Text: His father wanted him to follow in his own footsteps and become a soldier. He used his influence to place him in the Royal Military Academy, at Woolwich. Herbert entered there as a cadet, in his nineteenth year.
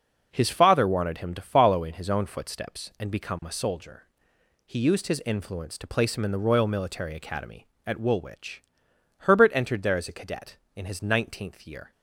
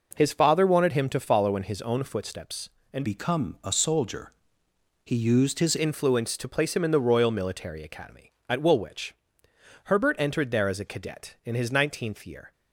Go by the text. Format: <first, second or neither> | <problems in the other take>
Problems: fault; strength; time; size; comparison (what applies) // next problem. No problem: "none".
first | changes voice from "become" to "his"; from 3.0 to 5.7 s; 2.7 s long